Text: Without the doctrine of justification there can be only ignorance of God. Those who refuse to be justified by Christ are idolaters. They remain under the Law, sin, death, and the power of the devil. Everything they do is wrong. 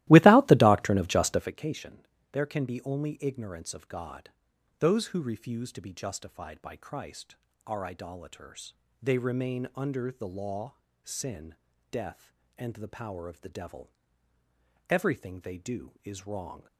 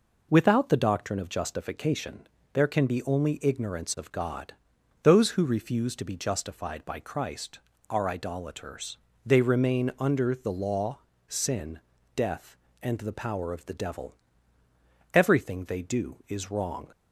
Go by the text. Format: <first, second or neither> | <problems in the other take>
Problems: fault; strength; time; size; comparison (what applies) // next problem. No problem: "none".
second | starts louder than the rest; strong; until 1.6 s; 16.5 dB // pauses between "justification" and "there"; slight; at 2.0 s; 0.26 s long; slight in the second